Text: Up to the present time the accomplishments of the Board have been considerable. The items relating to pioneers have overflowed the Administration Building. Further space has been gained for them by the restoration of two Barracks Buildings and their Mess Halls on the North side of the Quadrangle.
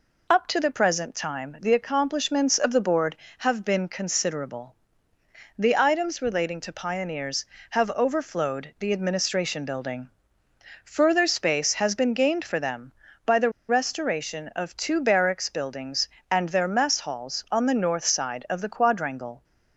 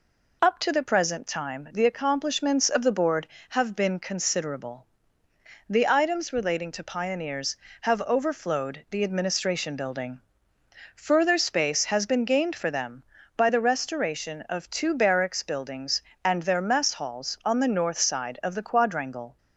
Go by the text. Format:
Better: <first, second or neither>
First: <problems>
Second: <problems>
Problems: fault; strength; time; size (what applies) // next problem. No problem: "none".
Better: second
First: pauses between "the" and "restoration"; slight; at 13.5 s; 0.18 s long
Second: none